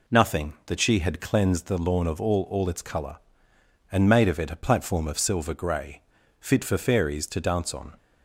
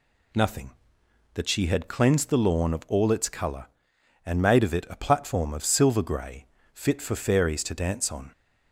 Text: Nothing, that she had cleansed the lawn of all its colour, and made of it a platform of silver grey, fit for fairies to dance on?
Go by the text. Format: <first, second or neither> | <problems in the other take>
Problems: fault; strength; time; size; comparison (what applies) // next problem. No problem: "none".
second | says "all" twice; at 2.4 s